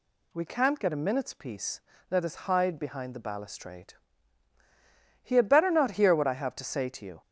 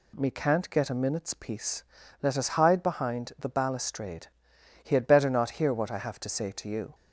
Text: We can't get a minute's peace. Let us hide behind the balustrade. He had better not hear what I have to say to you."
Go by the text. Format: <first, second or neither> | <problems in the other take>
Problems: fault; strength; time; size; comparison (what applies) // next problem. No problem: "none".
first | says "Me" for "We"; at 0.1 s